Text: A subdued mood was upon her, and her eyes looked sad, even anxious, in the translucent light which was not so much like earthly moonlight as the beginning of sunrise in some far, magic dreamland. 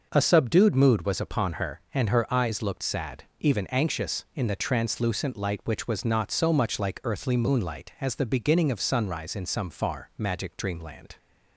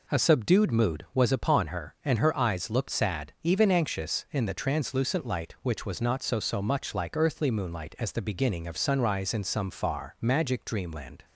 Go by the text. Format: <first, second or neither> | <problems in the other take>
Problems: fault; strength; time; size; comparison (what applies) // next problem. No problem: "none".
first | says "so" twice; at 6.3 s